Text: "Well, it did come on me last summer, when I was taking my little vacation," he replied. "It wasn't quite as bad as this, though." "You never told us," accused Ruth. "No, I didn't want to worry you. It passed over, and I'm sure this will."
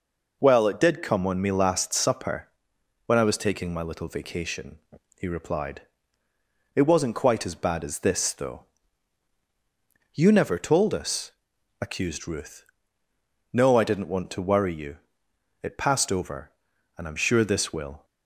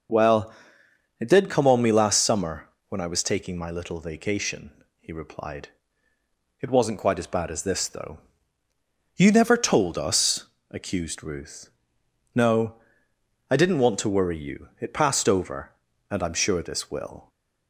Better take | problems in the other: second | says "supper" for "summer"; at 1.9 s

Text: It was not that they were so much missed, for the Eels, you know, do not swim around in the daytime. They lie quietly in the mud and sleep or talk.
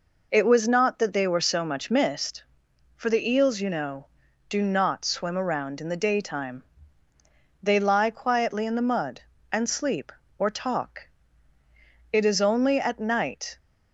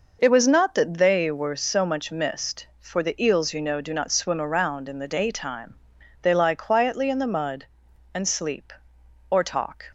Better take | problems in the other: second | goes on to say "It is only at night"; from 12.1 s on; 1.4 s long

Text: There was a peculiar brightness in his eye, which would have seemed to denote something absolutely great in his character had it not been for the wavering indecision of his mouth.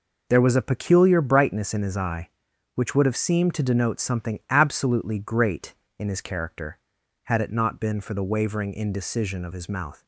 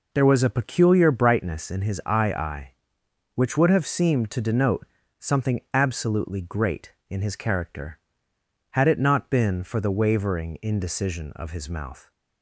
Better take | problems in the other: first | says "eye" twice; at 2.3 s // pauses between "denote" and "something"; slight; at 4.8 s; 0.36 s long

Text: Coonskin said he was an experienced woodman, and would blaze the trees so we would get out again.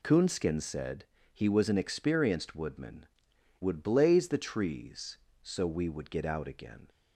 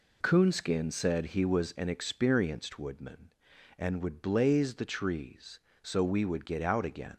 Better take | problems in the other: second | pauses between "said" and "he"; slight; at 1.0 s; 0.28 s long // skips "and"; at 3.3 s

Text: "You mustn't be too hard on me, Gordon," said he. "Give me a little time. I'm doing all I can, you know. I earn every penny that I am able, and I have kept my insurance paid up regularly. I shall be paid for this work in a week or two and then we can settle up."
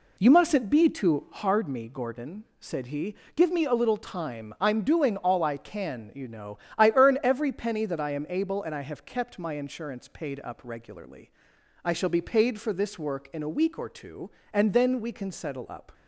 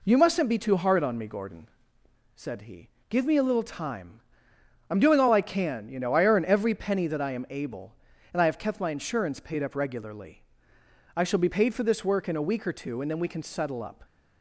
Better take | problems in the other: second | skips "on"; at 1.6 s

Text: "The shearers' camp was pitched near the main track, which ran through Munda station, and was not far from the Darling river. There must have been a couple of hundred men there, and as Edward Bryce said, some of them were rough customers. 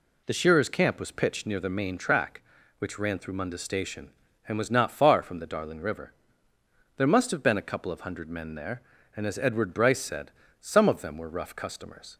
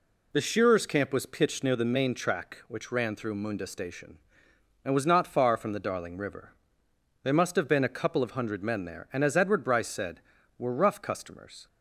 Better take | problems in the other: first | skips "some of them"; at 10.3 s

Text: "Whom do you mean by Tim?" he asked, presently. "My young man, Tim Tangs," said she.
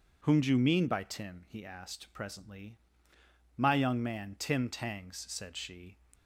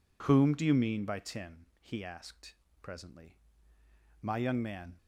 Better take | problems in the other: first | stops before "Tim Tangs said she"; at 4.9 s

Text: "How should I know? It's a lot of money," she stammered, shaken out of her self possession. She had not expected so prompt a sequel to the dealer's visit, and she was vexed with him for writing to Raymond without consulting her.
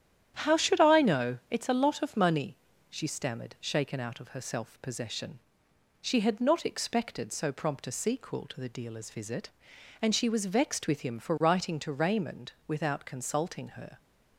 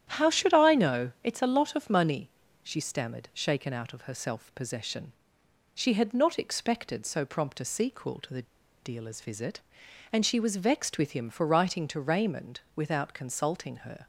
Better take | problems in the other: first | starts louder than the rest; strong; until 1.1 s; 10 dB; strong in the first // pauses between "the" and "dealer's"; at 8.4 s; 0.40 s long // pauses between "Raymond" and "without"; slight; at 12.5 s; 0.16 s long; slight in the first

